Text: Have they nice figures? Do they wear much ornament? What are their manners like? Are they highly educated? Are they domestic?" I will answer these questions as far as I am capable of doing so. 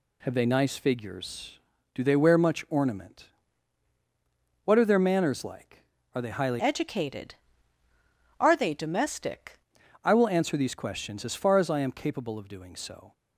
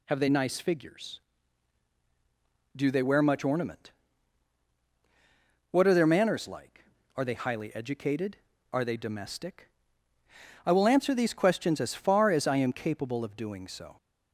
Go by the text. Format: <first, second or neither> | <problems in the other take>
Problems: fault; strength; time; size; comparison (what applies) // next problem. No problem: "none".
second | changes voice from "educated" to "domestic"; from 6.5 to 9.5 s; 3.0 s long